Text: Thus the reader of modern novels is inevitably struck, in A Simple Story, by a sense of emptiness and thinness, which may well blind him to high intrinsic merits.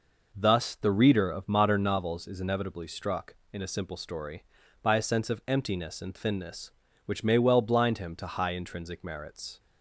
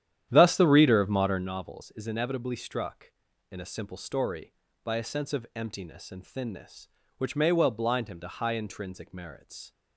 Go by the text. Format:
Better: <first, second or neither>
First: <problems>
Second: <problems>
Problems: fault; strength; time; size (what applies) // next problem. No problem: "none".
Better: first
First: none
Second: starts louder than the rest; strong; until 1.5 s; 10.5 dB